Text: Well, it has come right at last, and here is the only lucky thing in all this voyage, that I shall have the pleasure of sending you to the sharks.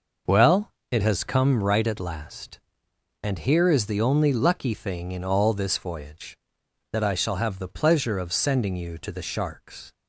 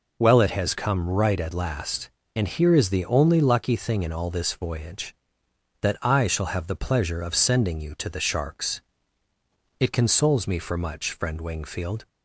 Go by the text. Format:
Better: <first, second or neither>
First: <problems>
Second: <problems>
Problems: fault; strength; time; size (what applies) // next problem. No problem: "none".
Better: first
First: none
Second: goes on to say "It consoles me for much friend Wingfield"; strong; from 9.7 s on; 2.2 s long